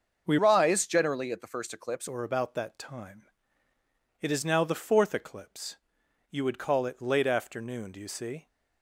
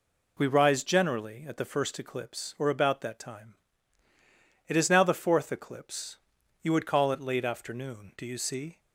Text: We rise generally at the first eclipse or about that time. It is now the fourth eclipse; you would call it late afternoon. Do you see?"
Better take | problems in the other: second | starts louder than the rest; until 1.2 s; 6.5 dB // changes voice from "rise" to "eclipse"; from 0.3 to 2.0 s; 1.7 s long

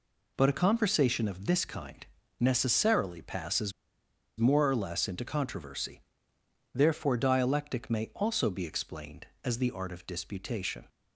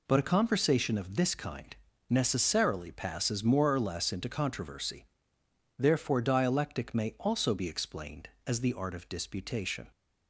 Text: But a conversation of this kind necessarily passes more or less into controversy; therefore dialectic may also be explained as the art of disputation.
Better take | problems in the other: second | pauses between "kind" and "necessarily"; slight; at 2.0 s; 0.36 s long; slight in the second // pauses between "passes" and "more"; noticeable; at 3.7 s; 0.66 s long

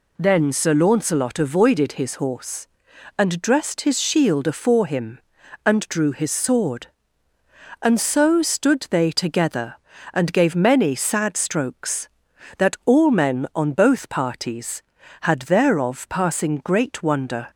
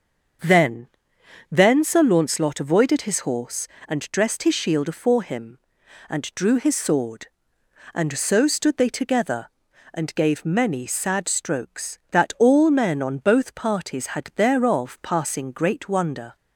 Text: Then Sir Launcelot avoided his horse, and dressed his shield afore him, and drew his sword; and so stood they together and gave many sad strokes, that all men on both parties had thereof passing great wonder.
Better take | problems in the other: first | starts louder than the rest; until 2.0 s; 7 dB // says "Then" twice; at 1.5 s

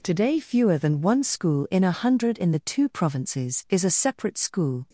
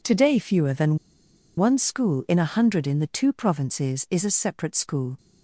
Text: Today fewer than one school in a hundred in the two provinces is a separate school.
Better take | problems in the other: first | pauses between "than" and "one"; noticeable; at 0.9 s; 0.59 s long

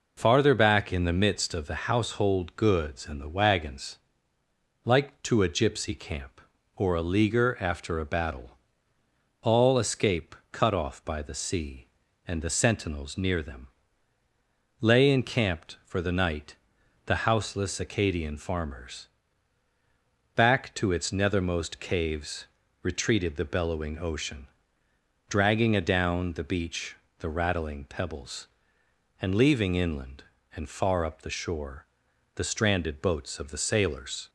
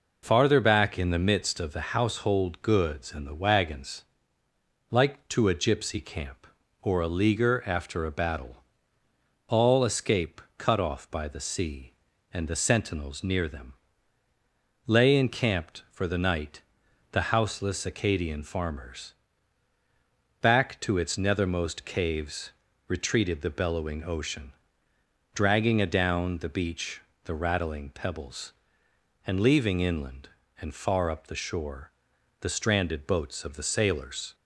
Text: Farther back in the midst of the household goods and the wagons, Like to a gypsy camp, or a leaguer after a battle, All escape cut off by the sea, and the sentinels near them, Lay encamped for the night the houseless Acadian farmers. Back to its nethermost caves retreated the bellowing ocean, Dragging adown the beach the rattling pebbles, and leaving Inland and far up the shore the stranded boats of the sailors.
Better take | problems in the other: neither | pauses between "escape" and "cut"; slight; the same in both // pauses between "night" and "the"; noticeable; the same in both // pauses between "caves" and "retreated"; slight; the same in both // pauses between "beach" and "the"; slight; the same in both // pauses between "shore" and "the"; noticeable; the same in both

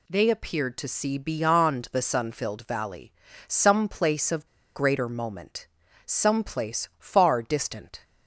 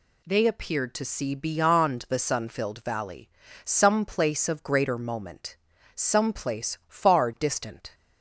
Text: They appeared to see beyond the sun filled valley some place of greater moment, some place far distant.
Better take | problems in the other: second | pauses between "valley" and "some"; slight; at 3.1 s; 0.36 s long; slight in the second // pauses between "of" and "greater"; slight; at 4.4 s; 0.29 s long

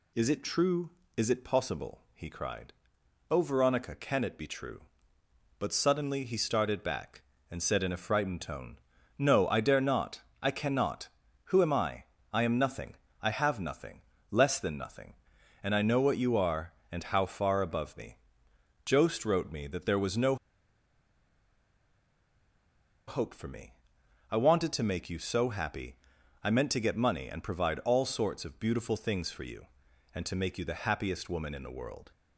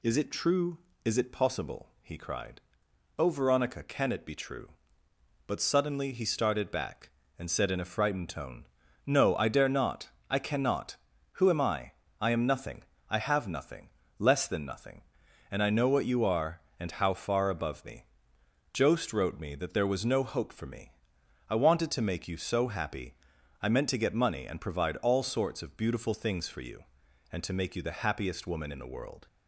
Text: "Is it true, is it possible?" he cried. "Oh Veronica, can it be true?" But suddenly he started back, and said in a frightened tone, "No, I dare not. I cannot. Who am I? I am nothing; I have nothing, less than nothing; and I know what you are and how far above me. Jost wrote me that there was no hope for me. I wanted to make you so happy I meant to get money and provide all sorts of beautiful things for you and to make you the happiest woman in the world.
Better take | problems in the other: second | pauses between "no" and "hope"; strong; at 20.3 s; 2.7 s long // pauses between "happy" and "I"; noticeable; at 25.9 s; 0.48 s long; noticeable in the second

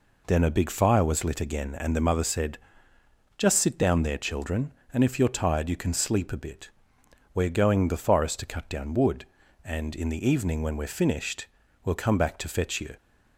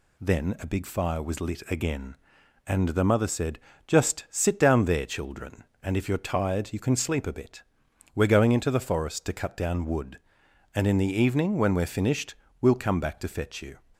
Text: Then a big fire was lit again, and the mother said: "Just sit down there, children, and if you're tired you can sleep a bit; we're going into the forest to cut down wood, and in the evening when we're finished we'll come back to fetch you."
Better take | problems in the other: second | skips "into"; at 7.8 s // pauses between "finished" and "we'll"; slight; at 11.4 s; 0.36 s long; slight in the second

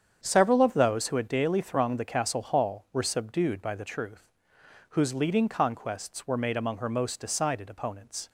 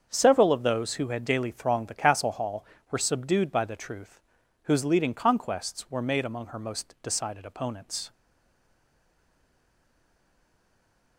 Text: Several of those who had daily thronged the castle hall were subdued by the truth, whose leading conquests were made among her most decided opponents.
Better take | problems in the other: first | starts louder than the rest; strong; until 1.1 s; 7 dB; strong in the first // stays silent after the last word; strong; from 8.1 s on; 3.0 s long

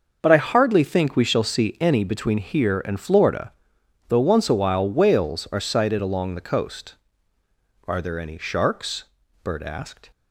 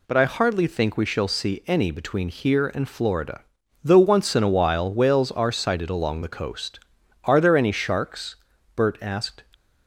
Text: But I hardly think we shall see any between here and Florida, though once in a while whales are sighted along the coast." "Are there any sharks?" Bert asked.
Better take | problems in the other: second | starts louder than the rest; until 1.2 s; 6 dB // skips "in"; at 4.5 s

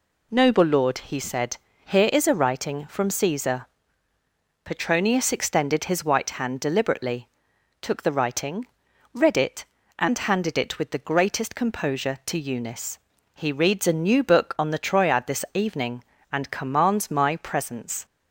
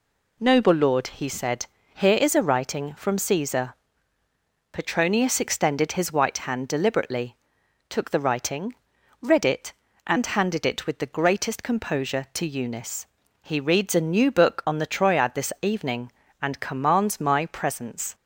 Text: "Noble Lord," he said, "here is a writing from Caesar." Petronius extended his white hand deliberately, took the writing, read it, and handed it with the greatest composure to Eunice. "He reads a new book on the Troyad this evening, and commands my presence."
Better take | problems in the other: neither | none

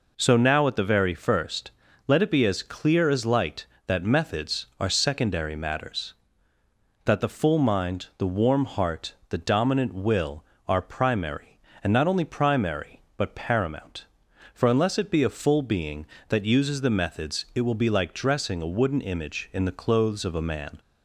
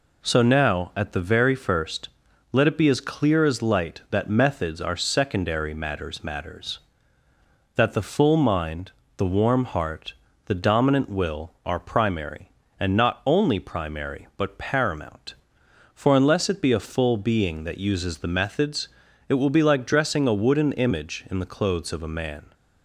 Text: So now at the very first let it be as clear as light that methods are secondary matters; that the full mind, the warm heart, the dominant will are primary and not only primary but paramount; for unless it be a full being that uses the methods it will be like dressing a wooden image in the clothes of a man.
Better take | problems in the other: first | pauses between "first" and "let"; at 2.0 s; 0.44 s long; slight in the first // says "matters" twice; at 6.2 s // pauses between "methods" and "it"; at 18.8 s; 0.38 s long

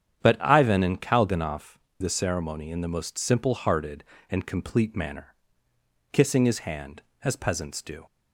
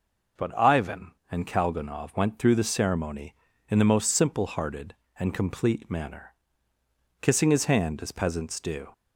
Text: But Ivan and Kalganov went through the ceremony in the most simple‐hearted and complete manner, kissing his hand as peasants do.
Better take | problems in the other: second | starts louder than the rest; strong; until 1.2 s; 9 dB; noticeable in the second // skips "went through"; at 1.8 s

